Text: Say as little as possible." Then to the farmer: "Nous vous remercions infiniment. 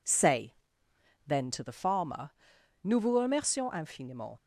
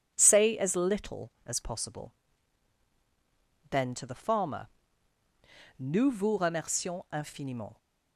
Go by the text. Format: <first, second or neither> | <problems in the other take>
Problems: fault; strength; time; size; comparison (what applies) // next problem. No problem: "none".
second | skips "as little as possible"; at 0.8 s